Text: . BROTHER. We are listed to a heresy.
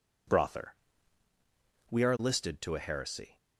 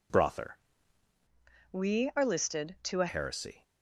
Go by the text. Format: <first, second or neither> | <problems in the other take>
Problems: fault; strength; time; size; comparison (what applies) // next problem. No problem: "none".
first | changes voice from "We" to "a"; from 1.7 to 3.0 s; 1.3 s long